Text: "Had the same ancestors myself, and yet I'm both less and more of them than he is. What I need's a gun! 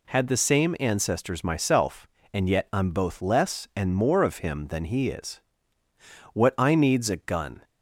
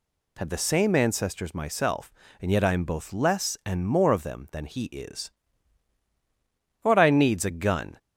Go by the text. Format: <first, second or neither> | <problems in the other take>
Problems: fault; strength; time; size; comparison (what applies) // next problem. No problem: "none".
second | says "him" for "them"; at 4.3 s